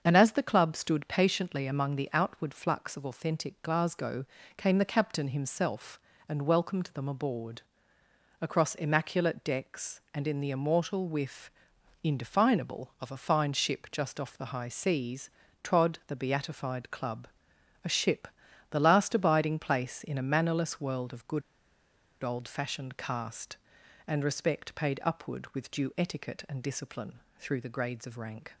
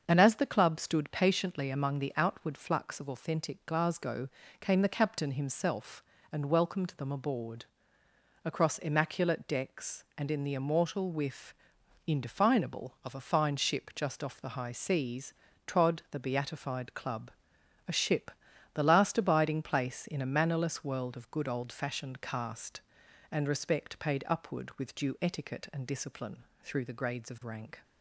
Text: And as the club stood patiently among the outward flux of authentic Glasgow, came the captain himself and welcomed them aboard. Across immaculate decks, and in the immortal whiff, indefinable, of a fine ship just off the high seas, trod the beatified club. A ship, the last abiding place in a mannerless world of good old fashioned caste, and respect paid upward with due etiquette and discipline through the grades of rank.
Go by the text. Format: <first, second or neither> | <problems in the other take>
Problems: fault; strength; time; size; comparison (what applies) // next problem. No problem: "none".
second | starts louder than the rest; until 1.0 s; 7 dB; also in the second // pauses between "good" and "old"; noticeable; at 21.4 s; 0.81 s long // pauses between "discipline" and "through"; slight; at 27.1 s; 0.18 s long; slight in the second